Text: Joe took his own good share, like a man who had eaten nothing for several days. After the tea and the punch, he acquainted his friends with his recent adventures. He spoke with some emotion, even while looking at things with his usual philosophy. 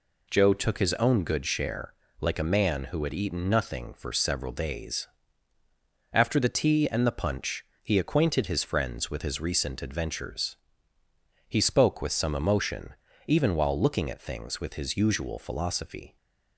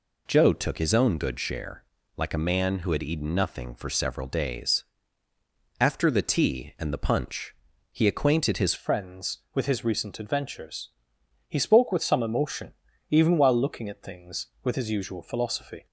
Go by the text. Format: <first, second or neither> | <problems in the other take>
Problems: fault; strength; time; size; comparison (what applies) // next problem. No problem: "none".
first | changes voice at "friends"; from 8.7 s on; 7.1 s long